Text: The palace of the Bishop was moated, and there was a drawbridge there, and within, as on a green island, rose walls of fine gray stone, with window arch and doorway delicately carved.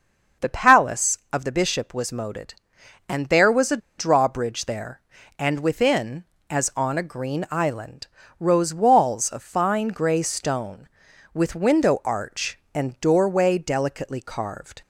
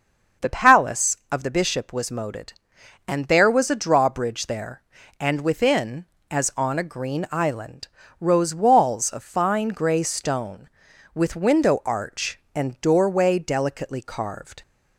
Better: second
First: starts louder than the rest; until 1.5 s; 6 dB // pauses between "a" and "drawbridge"; slight; at 3.7 s; 0.20 s long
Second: starts louder than the rest; until 1.5 s; 6 dB

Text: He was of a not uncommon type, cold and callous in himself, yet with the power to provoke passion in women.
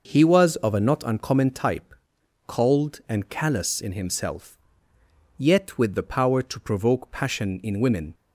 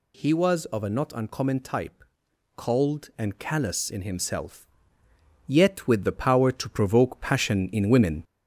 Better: first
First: none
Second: gets louder; slight; throughout; 3 dB

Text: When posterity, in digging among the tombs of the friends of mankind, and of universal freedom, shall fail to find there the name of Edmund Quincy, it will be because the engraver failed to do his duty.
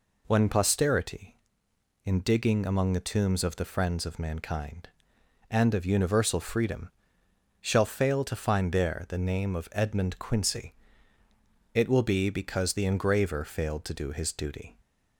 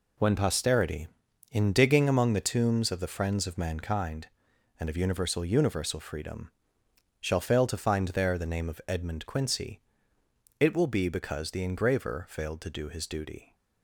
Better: first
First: none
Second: says "universal" twice; at 5.4 s

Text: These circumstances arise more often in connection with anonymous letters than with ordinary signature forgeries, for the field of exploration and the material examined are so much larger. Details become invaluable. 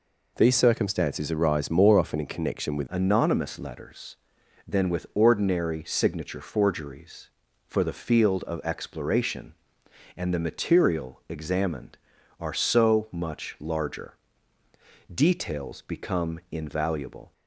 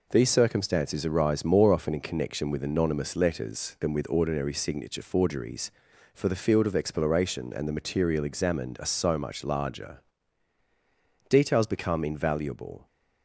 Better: second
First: changes voice at "anonymous"; from 2.8 s on; 14.5 s long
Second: none

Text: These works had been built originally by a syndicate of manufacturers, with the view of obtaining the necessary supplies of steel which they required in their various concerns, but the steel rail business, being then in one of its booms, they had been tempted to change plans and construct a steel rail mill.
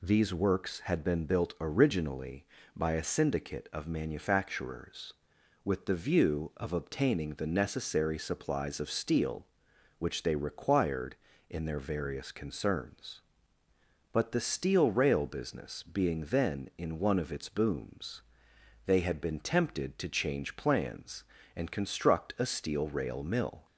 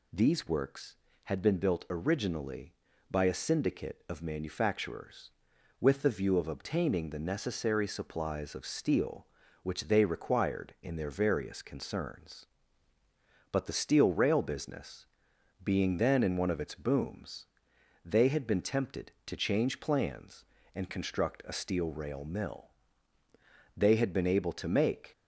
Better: first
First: none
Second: goes on to say "They had been able to make"; from 23.7 s on; 1.3 s long

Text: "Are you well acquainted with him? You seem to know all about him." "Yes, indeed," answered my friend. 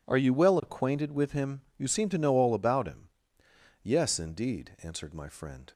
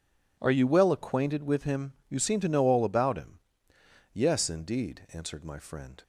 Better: neither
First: none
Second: none

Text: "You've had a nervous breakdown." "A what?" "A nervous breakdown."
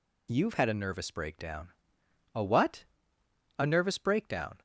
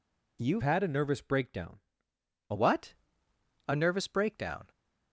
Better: first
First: none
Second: changes voice from "had" to "A"; from 0.6 to 2.5 s; 1.9 s long

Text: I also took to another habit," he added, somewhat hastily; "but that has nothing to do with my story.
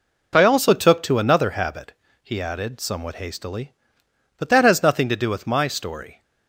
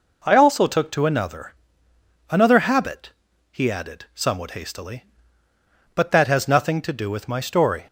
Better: first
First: none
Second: says "another" twice; at 2.3 s

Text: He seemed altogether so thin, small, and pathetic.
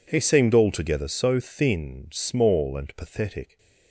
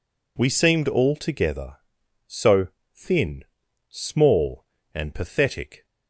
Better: first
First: none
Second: says "We" for "He"; at 0.3 s // pauses between "so" and "thin"; slight; at 2.6 s; 0.24 s long

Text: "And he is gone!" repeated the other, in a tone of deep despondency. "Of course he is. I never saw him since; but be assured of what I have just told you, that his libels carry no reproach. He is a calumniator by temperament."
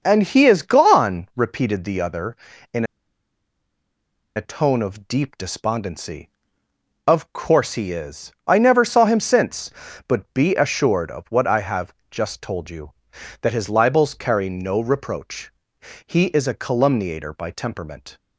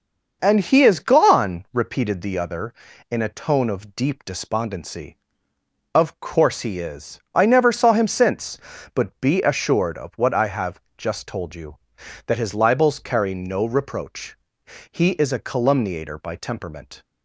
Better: second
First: starts louder than the rest; until 1.0 s; 6 dB // pauses between "in" and "a"; strong; at 2.8 s; 1.5 s long // pauses between "have" and "just"; slight; at 11.9 s; 0.16 s long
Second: starts louder than the rest; until 1.4 s; 6 dB // pauses between "have" and "just"; slight; at 10.7 s; 0.16 s long

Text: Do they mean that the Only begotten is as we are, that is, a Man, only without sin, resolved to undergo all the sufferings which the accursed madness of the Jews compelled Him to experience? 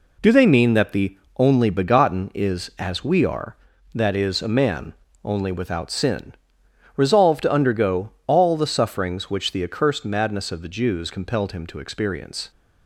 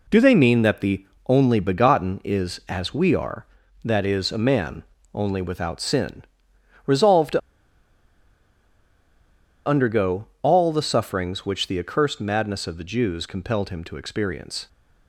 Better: first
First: pauses between "the" and "Only"; slight; at 1.1 s; 0.18 s long // pauses between "undergo" and "all"; slight; at 8.1 s; 0.16 s long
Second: pauses between "the" and "Only"; slight; at 1.0 s; 0.20 s long // pauses between "to" and "undergo"; strong; at 7.4 s; 2.2 s long // pauses between "undergo" and "all"; slight; at 10.2 s; 0.16 s long

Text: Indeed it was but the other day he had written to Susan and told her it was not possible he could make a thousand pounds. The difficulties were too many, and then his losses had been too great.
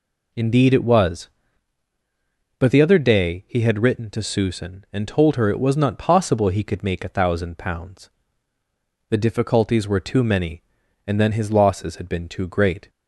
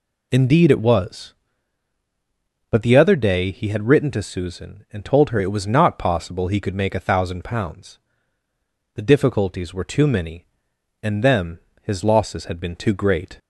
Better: first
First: none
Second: says "them" for "then"; at 11.2 s

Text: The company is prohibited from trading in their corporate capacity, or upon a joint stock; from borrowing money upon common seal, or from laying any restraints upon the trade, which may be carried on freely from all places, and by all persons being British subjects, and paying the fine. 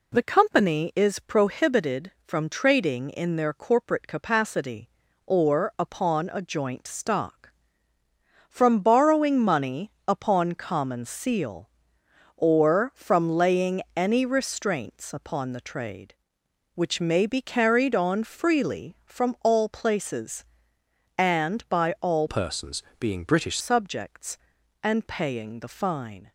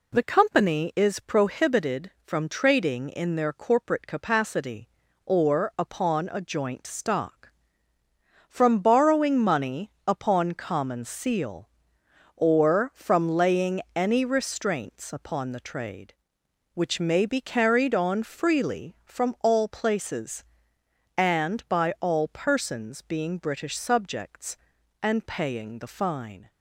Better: second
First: pauses between "money" and "upon"; slight; at 9.8 s; 0.18 s long // pauses between "laying" and "any"; slight; at 13.8 s; 0.16 s long // changes voice from "persons" to "British"; from 22.2 to 23.5 s; 1.3 s long // pauses between "persons" and "being"; slight; at 22.8 s; 0.18 s long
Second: pauses between "money" and "upon"; slight; at 9.8 s; 0.18 s long // pauses between "laying" and "any"; slight; at 13.8 s; 0.16 s long

